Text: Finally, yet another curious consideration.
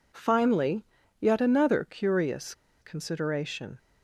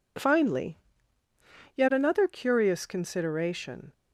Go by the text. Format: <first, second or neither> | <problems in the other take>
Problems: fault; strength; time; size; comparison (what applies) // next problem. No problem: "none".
second | pauses between "curious" and "consideration"; slight; at 2.5 s; 0.29 s long